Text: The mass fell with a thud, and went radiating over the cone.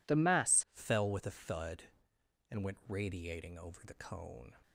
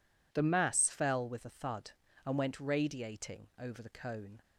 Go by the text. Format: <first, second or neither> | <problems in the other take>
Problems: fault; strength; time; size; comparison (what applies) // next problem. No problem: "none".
second | changes voice at "fell"; from 0.7 s on; 3.8 s long